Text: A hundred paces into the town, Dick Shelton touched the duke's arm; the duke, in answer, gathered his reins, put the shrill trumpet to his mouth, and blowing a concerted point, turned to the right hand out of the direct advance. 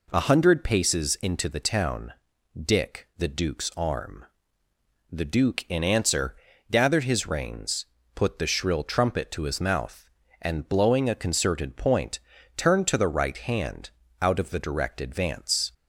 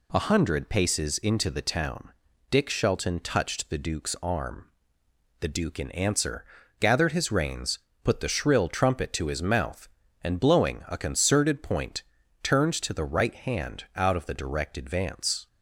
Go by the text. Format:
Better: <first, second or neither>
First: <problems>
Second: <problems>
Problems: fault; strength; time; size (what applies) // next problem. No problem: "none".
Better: second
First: skips "Shelton touched"; at 3.1 s // pauses between "hand" and "out"; slight; at 13.9 s; 0.28 s long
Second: none